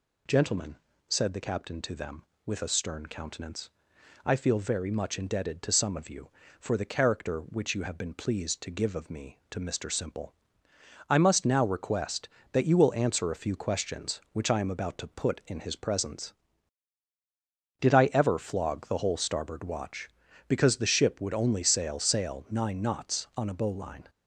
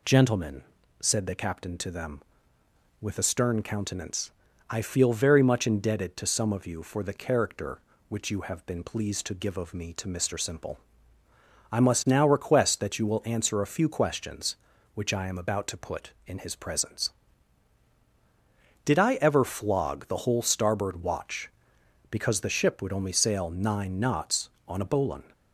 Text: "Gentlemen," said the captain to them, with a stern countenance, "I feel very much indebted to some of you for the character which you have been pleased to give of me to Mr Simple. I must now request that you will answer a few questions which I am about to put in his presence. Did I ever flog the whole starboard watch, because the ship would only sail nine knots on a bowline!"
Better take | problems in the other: second | says "sail" twice; at 21.9 s

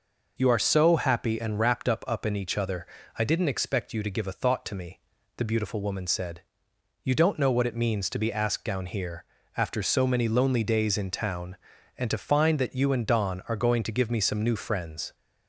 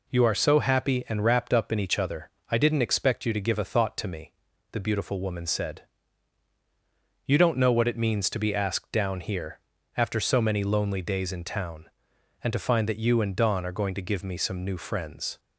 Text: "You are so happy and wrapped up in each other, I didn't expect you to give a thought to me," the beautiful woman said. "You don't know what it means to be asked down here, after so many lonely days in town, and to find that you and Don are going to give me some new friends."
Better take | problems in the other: second | says "up" twice; at 2.0 s

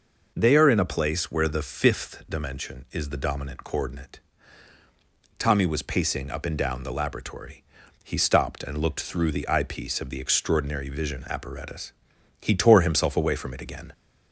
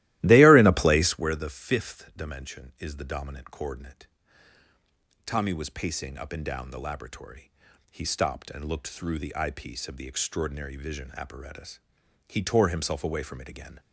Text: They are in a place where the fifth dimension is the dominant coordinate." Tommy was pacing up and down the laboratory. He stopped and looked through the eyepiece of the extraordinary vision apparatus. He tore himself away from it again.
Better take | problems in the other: first | starts louder than the rest; strong; until 1.4 s; 16 dB

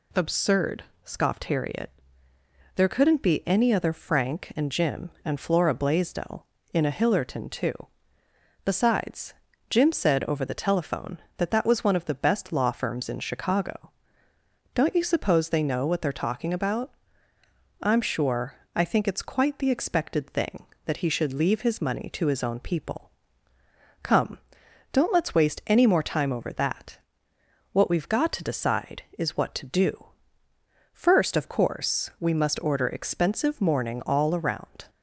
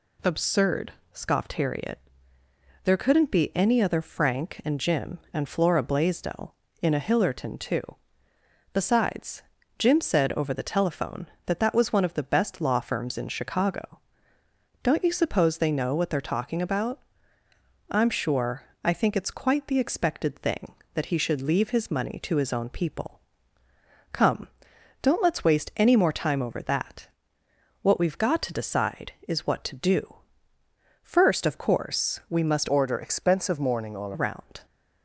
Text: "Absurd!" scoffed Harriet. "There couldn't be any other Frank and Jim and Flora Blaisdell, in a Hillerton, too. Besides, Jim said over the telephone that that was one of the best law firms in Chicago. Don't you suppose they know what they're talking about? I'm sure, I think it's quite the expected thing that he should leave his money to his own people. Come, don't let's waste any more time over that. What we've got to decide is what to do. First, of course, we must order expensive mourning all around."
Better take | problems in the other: first | changes voice from "order" to "all"; from 32.6 to 34.1 s; 1.5 s long

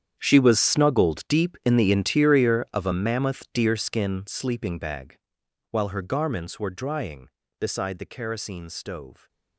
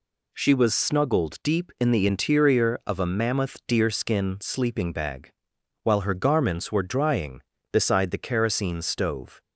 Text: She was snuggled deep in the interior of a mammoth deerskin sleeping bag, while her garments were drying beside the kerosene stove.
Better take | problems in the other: second | gets quieter; strong; throughout; 17.5 dB

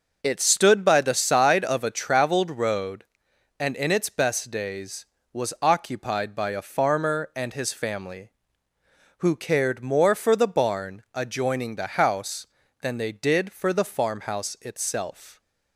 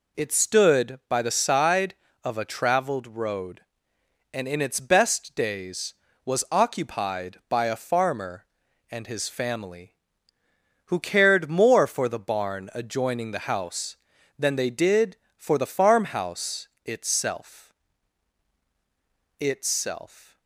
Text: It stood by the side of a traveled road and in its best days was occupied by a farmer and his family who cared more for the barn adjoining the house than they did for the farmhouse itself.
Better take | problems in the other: first | pauses between "farmhouse" and "itself"; slight; at 16.6 s; 0.18 s long // says "itself" twice; at 19.3 s

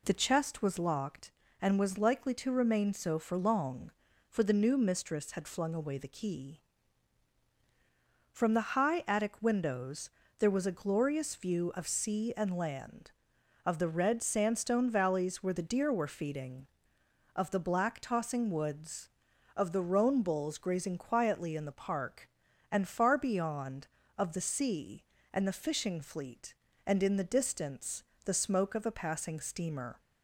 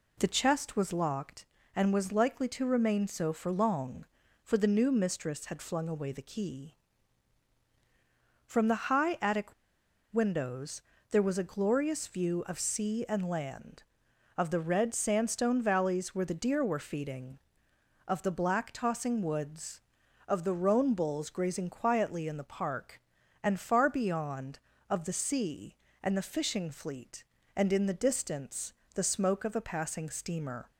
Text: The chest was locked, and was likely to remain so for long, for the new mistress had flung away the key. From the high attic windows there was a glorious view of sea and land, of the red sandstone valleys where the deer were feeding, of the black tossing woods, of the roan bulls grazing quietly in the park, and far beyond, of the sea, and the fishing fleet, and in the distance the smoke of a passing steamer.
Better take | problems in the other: first | pauses between "attic" and "windows"; noticeable; at 9.5 s; 0.57 s long // pauses between "windows" and "there"; slight; at 10.8 s; 0.30 s long; slight in the first // pauses between "distance" and "the"; slight; at 28.7 s; 0.20 s long; slight in the first

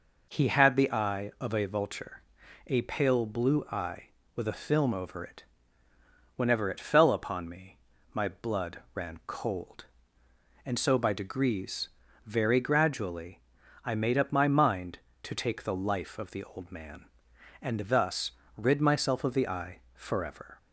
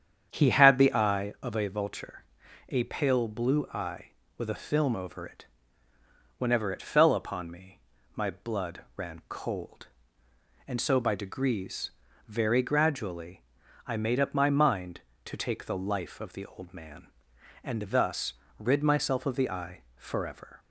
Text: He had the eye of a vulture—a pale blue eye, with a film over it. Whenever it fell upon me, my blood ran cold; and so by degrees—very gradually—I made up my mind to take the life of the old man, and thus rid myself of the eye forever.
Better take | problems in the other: first | starts louder than the rest; strong; until 1.4 s; 8.5 dB // pauses between "thus" and "rid"; slight; at 18.3 s; 0.24 s long; slight in the first // pauses between "eye" and "forever"; slight; at 19.8 s; 0.16 s long; slight in the first

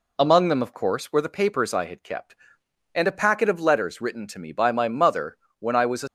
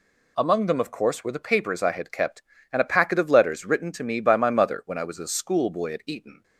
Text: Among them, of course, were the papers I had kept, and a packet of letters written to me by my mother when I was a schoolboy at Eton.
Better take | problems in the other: second | pauses between "mother" and "when"; slight; at 5.3 s; 0.22 s long // stops before "schoolboy at Eton"; at 6.0 s

